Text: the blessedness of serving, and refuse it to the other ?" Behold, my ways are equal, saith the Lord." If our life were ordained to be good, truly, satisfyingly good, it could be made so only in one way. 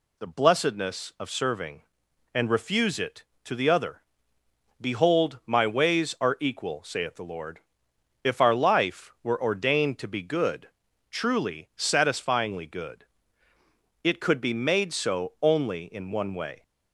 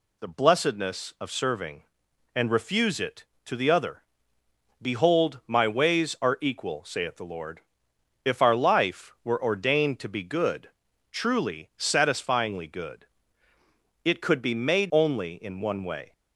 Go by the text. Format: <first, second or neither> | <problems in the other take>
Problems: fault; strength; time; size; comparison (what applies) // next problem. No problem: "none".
first | skips "so"; at 14.9 s